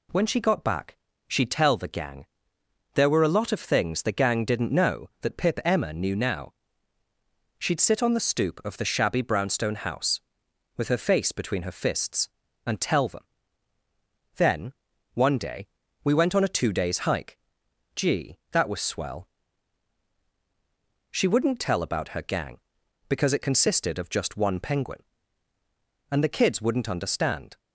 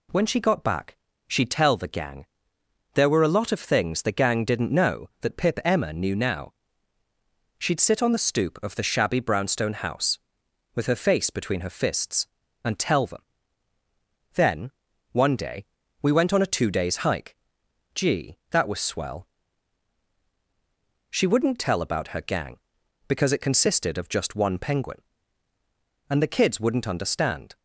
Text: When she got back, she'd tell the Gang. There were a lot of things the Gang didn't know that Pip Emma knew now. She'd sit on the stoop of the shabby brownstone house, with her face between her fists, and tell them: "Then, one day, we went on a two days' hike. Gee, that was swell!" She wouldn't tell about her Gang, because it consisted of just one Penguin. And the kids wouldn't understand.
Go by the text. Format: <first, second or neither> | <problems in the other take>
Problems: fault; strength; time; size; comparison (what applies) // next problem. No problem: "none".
neither | none